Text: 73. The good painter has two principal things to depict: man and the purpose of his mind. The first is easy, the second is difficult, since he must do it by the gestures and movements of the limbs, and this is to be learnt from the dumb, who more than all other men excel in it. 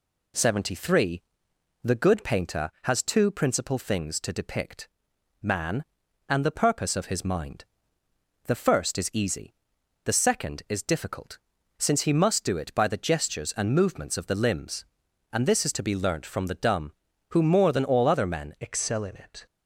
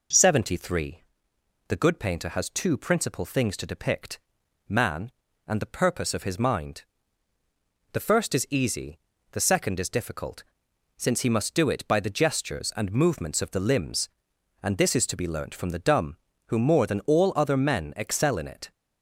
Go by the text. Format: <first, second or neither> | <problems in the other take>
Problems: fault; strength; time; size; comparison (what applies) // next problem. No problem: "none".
second | changes voice at "excel"; from 18.5 s on; 0.9 s long